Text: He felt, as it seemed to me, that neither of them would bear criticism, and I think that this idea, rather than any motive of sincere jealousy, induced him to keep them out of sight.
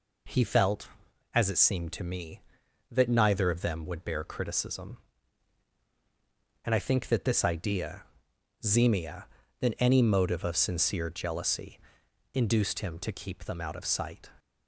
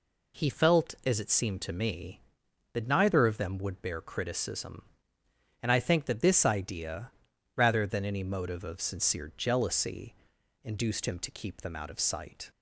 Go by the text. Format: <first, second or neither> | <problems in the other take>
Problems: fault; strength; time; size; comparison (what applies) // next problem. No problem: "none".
second | says "zemia" for "rather"; at 8.6 s